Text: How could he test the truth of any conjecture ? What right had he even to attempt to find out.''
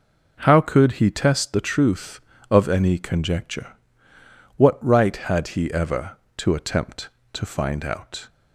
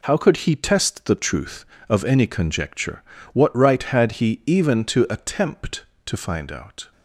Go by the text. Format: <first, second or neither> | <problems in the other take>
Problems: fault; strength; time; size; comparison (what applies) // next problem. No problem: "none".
second | says "ever" for "even"; at 5.7 s